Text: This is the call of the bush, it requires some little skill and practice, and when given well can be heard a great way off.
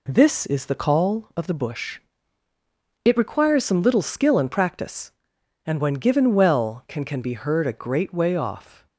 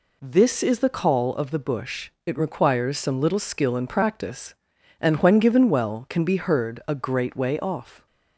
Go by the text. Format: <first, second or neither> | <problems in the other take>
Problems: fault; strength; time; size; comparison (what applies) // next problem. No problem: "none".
second | says "can" twice; at 7.0 s